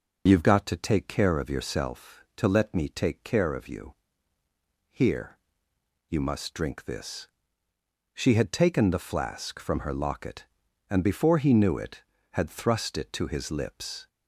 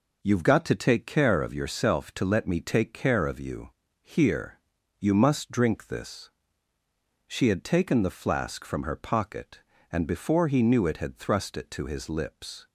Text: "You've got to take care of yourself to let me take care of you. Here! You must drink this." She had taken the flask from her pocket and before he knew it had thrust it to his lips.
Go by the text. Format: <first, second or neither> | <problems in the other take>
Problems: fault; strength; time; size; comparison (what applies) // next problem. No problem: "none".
second | says "locket" for "pocket"; at 9.9 s